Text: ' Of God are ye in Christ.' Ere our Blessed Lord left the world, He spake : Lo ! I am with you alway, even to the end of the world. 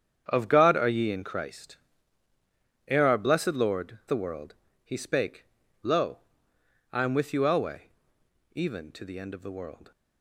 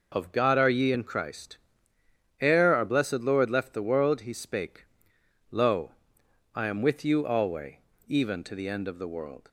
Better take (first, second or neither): second